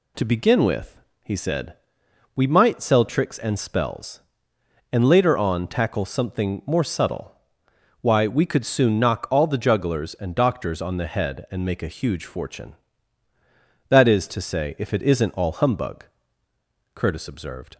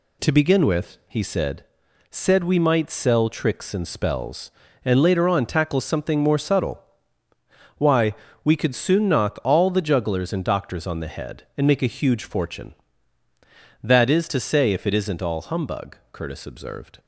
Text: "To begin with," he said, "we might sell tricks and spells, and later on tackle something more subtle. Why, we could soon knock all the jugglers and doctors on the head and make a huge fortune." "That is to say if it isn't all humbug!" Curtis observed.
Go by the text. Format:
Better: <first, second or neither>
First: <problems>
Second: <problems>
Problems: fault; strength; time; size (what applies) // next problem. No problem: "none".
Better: first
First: none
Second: says "said" twice; at 2.1 s